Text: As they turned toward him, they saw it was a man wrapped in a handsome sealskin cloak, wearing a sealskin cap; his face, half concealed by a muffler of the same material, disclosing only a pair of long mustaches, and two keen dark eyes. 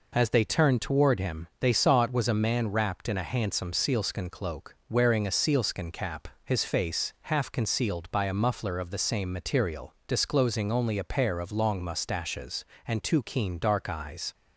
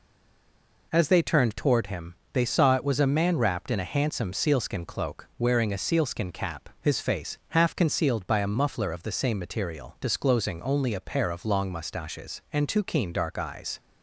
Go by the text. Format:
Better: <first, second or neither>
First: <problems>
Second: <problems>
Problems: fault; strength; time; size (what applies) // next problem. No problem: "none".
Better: first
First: none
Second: stays silent before the first word; slight; until 0.9 s; 0.9 s long